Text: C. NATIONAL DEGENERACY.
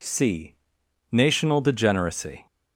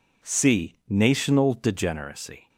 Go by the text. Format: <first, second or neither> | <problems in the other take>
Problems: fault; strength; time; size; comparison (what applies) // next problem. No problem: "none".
neither | none